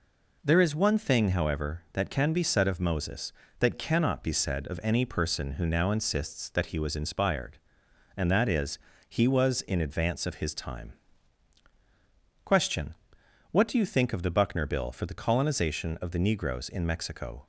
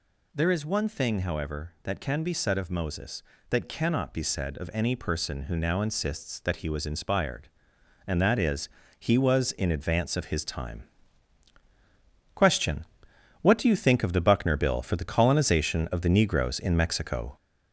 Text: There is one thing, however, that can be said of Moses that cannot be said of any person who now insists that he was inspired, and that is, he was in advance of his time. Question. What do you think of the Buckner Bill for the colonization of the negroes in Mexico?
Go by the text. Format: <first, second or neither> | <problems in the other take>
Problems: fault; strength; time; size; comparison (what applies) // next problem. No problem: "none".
first | gets louder; noticeable; throughout; 5 dB